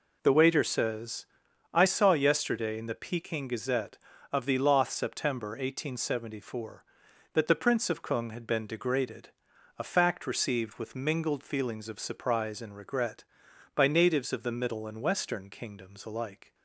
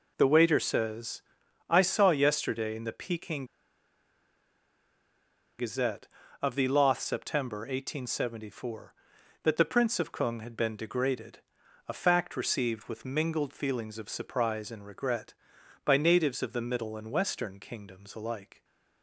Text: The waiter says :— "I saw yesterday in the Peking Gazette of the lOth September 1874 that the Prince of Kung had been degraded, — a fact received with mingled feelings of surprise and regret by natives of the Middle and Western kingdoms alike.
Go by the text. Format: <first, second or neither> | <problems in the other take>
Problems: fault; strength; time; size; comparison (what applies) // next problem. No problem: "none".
first | pauses between "Peking" and "Gazette"; strong; at 3.4 s; 2.1 s long